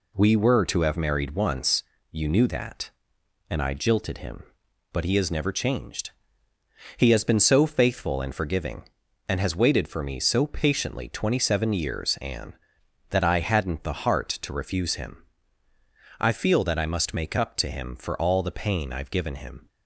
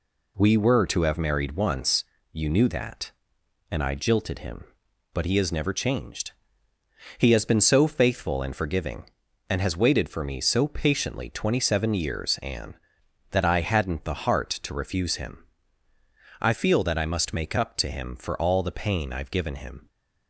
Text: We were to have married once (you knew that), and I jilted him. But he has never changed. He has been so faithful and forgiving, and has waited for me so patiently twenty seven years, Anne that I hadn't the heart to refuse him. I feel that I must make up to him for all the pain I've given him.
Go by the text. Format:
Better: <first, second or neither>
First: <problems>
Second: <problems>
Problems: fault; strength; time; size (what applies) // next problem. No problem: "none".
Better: neither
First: none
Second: none